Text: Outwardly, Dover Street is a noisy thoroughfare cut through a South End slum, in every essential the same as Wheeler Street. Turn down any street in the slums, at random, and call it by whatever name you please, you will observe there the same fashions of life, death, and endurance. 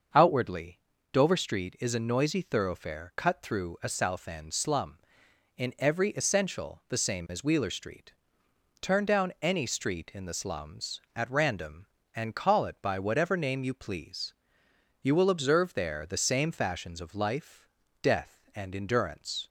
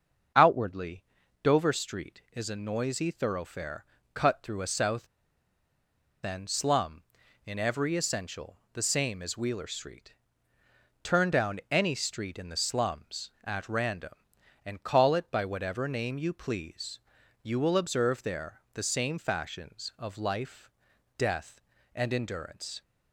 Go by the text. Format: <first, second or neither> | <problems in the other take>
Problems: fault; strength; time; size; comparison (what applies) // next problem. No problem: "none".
first | starts louder than the rest; until 1.7 s; 6.5 dB; also in the first // pauses between "thoroughfare" and "cut"; slight; at 3.8 s; 0.28 s long // pauses between "South" and "End"; at 5.0 s; 1.1 s long // pauses between "essential" and "the"; slight; at 8.5 s; 0.16 s long